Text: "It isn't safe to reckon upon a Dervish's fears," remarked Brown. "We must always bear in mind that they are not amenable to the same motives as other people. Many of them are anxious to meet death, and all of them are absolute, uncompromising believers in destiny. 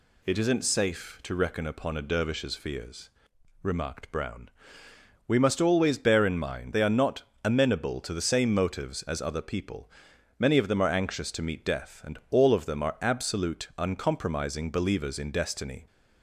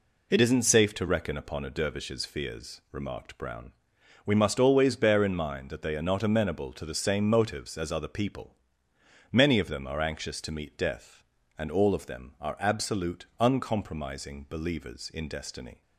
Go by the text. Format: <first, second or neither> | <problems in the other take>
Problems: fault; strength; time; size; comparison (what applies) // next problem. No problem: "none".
second | skips "that"; at 6.7 s // pauses between "not" and "amenable"; slight; at 7.2 s; 0.20 s long